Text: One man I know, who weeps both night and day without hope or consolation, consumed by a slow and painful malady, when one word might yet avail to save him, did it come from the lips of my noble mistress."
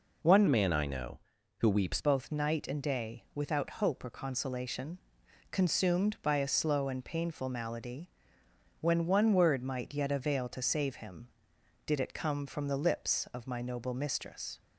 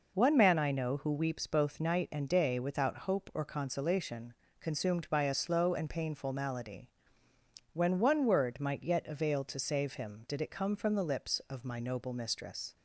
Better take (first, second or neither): second